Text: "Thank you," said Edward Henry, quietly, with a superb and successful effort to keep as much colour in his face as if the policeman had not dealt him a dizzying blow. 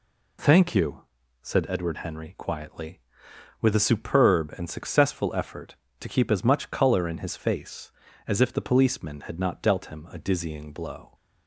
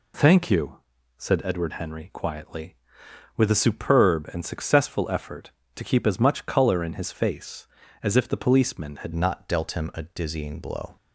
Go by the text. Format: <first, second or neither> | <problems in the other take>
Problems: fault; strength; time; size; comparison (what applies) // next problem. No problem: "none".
first | changes voice at "not"; from 9.1 s on; 1.8 s long